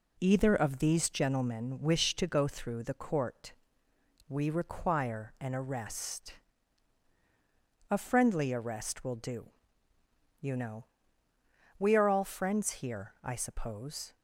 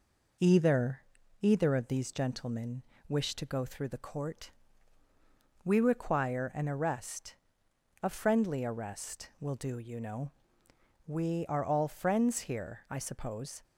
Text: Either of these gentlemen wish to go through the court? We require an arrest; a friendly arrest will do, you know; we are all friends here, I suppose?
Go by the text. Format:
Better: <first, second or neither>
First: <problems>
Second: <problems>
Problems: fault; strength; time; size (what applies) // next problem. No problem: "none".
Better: first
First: none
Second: says "Either" twice; at 1.4 s // pauses between "gentlemen" and "wish"; slight; at 2.8 s; 0.26 s long